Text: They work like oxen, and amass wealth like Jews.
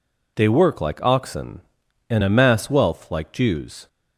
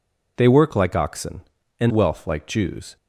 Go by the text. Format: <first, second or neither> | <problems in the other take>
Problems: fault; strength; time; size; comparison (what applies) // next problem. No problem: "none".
first | skips "amass"; at 1.9 s